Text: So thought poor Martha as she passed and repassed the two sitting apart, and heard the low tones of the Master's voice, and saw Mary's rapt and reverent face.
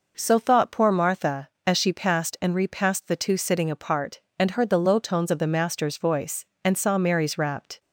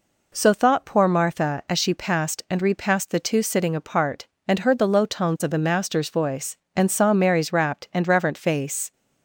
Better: second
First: stops before "and reverent face"; at 7.7 s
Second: none

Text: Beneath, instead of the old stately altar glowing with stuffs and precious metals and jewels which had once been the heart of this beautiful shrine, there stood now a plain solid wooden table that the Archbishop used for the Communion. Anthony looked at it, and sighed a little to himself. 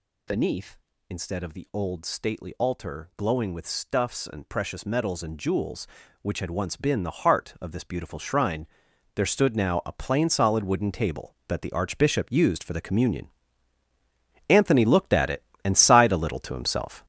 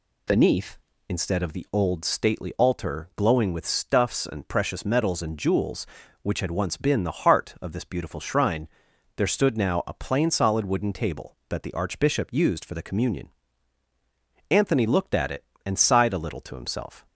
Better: second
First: gets louder; throughout; 7 dB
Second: none

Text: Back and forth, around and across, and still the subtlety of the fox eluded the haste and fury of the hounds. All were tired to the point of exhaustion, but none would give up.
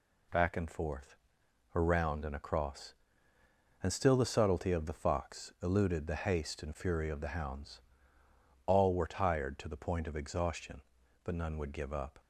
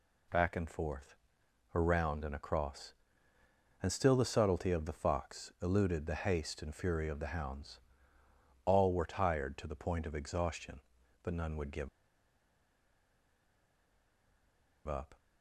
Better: first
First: none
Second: pauses between "give" and "up"; strong; at 11.8 s; 2.9 s long

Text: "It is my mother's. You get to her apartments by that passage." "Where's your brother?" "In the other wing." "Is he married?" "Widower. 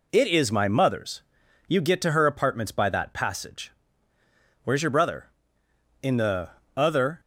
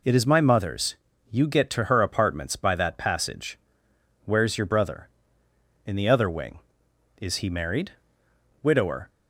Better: second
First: pauses between "the" and "other"; slight; at 6.4 s; 0.26 s long // stops before "wing Is he married Widower"; at 7.1 s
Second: none

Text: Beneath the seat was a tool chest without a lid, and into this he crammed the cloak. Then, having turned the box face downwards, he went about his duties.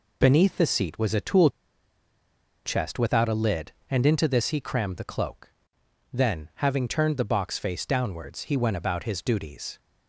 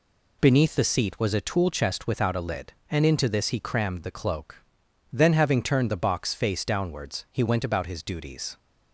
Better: second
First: pauses between "tool" and "chest"; at 1.5 s; 1.1 s long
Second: none

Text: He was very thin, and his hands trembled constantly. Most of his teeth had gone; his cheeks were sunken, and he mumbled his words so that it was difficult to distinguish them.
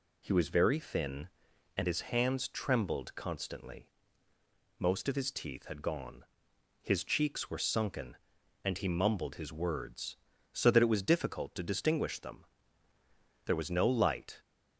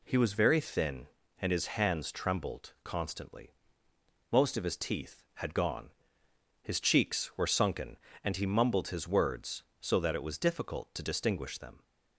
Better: second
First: goes on to say "There was no light"; noticeable; from 13.4 s on; 0.96 s long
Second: none

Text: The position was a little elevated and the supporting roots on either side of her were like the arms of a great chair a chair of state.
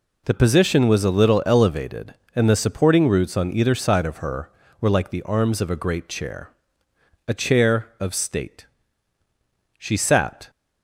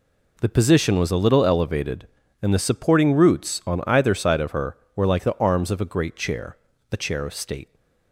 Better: second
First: pauses between "chair" and "a"; noticeable; at 6.4 s; 0.76 s long // goes on to say "She sat"; noticeable; from 9.7 s on; 0.72 s long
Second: pauses between "chair" and "a"; slight; at 6.5 s; 0.36 s long

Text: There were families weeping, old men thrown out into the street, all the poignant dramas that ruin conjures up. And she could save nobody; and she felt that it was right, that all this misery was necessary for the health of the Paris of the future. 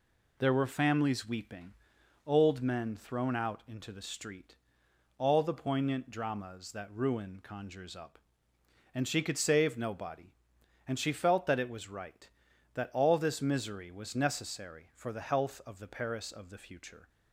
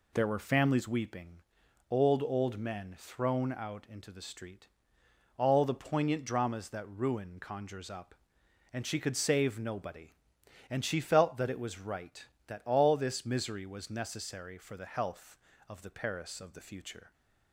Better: first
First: none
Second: says "old" twice; at 2.2 s

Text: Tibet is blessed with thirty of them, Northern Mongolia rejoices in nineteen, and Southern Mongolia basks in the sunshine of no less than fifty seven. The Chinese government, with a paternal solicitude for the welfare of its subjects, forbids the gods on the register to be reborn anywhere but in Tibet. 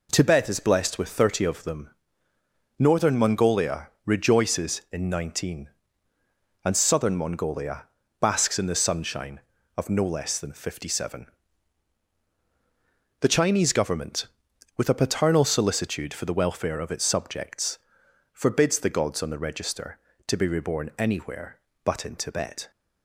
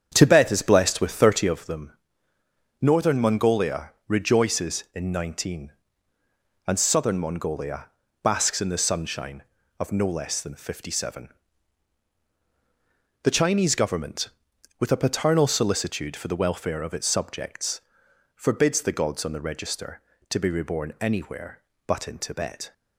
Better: first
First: pauses between "Mongolia" and "basks"; slight; at 7.8 s; 0.34 s long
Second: starts louder than the rest; strong; until 1.5 s; 8 dB // pauses between "Mongolia" and "basks"; slight; at 7.8 s; 0.34 s long

